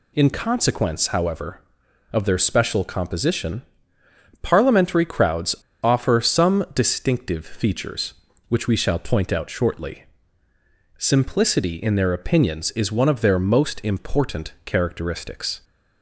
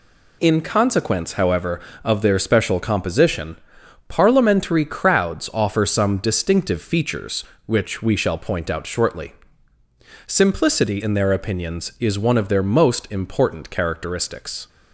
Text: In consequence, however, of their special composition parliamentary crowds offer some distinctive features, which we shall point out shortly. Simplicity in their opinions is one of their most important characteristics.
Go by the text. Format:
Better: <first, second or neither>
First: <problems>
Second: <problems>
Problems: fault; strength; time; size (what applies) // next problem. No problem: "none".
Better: second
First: pauses between "composition" and "parliamentary"; noticeable; at 3.6 s; 0.80 s long // pauses between "crowds" and "offer"; slight; at 5.5 s; 0.26 s long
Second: pauses between "composition" and "parliamentary"; noticeable; at 3.5 s; 0.52 s long